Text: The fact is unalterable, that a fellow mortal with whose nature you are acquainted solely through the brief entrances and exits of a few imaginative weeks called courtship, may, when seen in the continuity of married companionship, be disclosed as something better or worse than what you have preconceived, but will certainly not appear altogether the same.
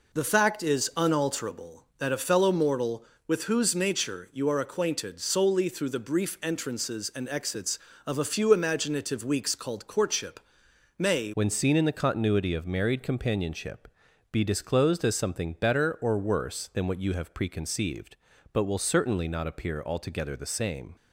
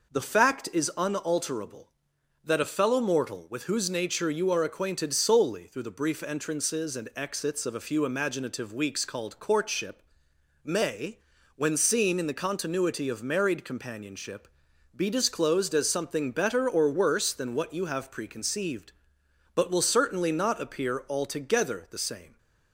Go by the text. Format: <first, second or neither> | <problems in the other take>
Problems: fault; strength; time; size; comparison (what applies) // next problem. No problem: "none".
second | changes voice at "when"; from 11.3 s on; 9.6 s long